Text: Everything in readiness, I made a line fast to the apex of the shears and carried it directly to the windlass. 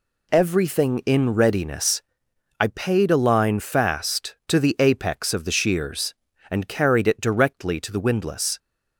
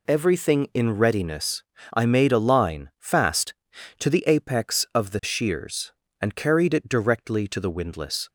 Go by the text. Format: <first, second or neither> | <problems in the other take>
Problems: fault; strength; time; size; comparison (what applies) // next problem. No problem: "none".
second | says "paid" for "made"; at 2.6 s